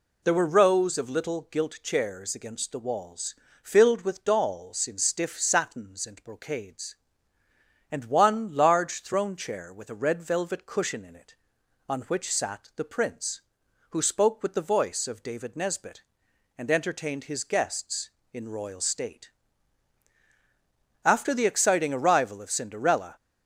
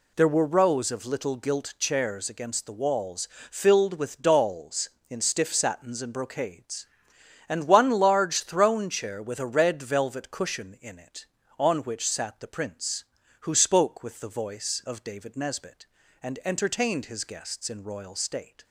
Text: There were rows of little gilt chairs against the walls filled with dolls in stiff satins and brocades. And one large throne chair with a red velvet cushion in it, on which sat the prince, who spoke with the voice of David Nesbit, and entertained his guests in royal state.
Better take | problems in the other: second | pauses between "walls" and "filled"; slight; at 3.3 s; 0.26 s long; slight in the second // goes on to say "After the exciting arrival of Cinderella"; strong; from 21.0 s on; 2.1 s long

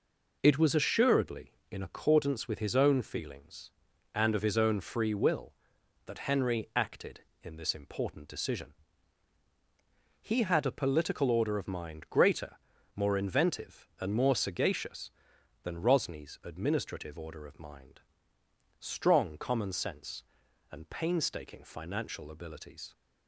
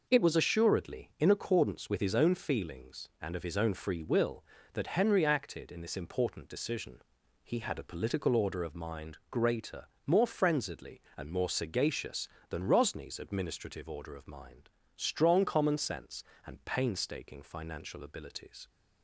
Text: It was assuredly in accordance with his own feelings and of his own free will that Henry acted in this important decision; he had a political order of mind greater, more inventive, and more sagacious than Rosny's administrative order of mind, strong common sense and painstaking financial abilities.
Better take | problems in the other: first | says "frenziedly" for "inventive"; at 10.2 s

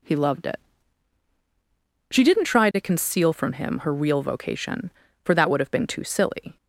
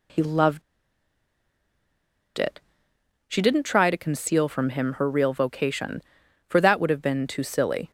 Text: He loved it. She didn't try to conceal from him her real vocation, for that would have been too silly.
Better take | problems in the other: first | pauses between "loved" and "it"; strong; at 0.6 s; 1.7 s long

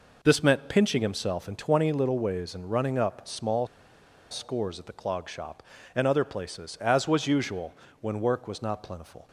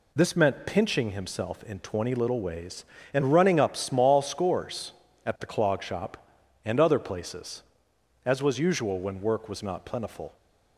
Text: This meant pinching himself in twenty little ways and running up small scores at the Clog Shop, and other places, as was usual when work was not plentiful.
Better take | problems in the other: second | pauses between "small" and "scores"; noticeable; at 3.6 s; 0.65 s long // pauses between "usual" and "when"; slight; at 7.7 s; 0.28 s long

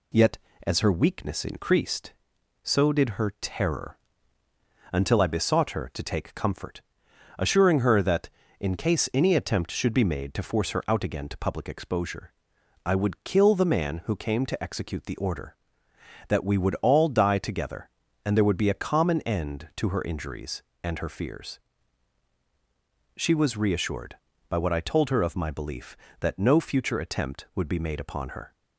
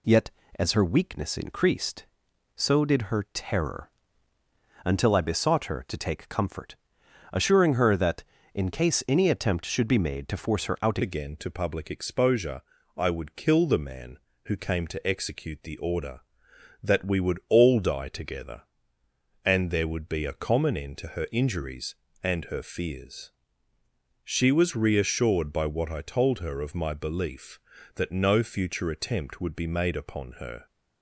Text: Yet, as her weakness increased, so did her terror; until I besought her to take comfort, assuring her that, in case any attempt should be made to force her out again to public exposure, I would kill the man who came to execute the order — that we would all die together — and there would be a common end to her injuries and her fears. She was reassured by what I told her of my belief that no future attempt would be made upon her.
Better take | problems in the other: first | changes voice at "again"; from 11.0 s on; 19.6 s long

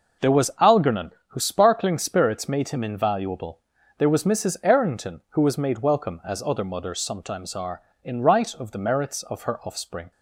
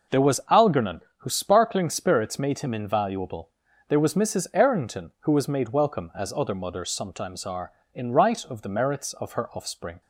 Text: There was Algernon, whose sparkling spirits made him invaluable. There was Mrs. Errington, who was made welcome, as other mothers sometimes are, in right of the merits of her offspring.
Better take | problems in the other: neither | none

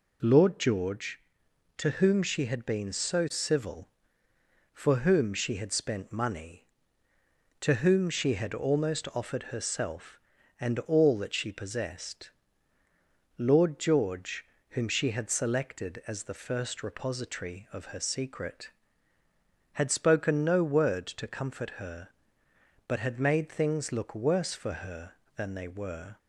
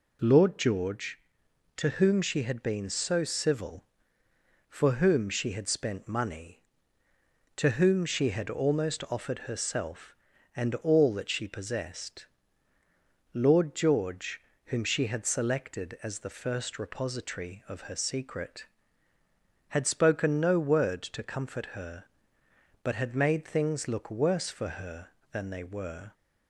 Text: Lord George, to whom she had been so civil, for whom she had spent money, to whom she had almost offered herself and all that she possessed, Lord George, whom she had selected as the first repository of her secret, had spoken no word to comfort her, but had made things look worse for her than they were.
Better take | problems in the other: neither | none

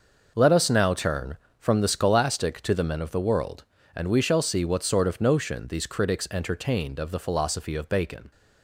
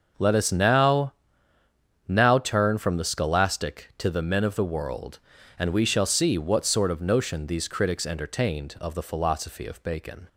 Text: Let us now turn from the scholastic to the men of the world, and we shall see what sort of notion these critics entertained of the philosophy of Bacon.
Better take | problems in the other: first | starts louder than the rest; noticeable; until 2.1 s; 6 dB; noticeable in the first // says "now" twice; at 2.0 s

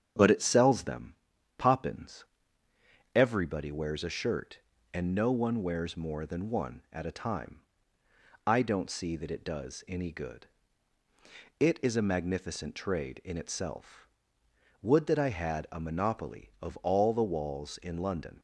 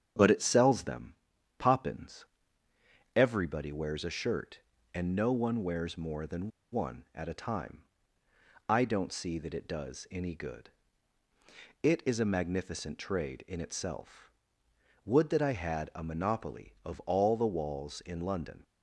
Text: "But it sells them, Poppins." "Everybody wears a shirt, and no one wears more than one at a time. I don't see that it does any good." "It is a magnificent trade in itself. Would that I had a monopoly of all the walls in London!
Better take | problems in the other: first | starts louder than the rest; strong; until 1.6 s; 8 dB; strong in the first // pauses between "than" and "one"; slight; at 6.4 s; 0.23 s long

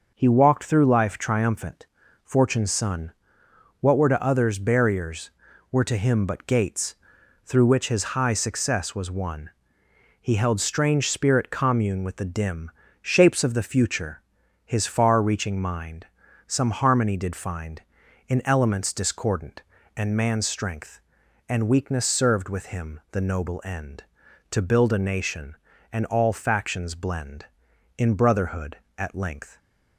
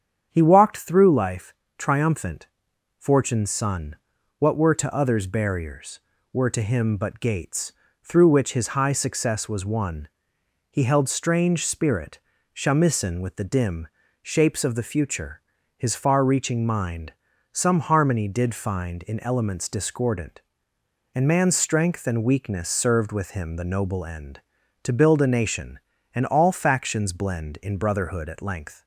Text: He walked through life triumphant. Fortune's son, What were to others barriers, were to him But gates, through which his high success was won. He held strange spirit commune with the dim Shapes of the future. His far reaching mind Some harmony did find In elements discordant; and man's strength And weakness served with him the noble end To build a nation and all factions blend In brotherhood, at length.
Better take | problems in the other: first | starts louder than the rest; strong; until 1.3 s; 8 dB; noticeable in the first // pauses between "life" and "triumphant"; slight; at 1.5 s; 0.24 s long // says "shamisen" for "commune"; at 12.5 s // pauses between "dim" and "Shapes"; slight; at 13.8 s; 0.34 s long; slight in the first // pauses between "mind" and "Some"; at 17.1 s; 0.38 s long; also in the first

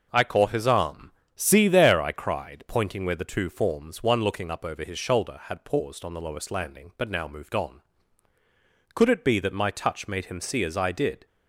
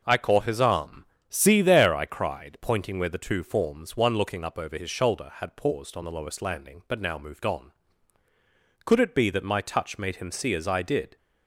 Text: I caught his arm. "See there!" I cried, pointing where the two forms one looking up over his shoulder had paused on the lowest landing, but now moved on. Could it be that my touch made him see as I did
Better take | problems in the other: neither | none

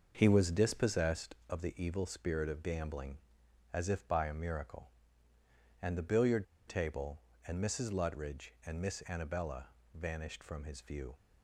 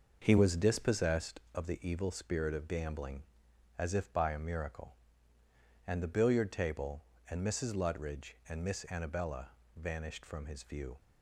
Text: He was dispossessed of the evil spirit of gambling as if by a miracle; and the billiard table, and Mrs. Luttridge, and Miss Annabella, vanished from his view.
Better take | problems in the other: second | starts louder than the rest; noticeable; until 1.1 s; 6 dB; noticeable in the second // pauses between "billiard" and "table"; slight; at 6.4 s; 0.22 s long

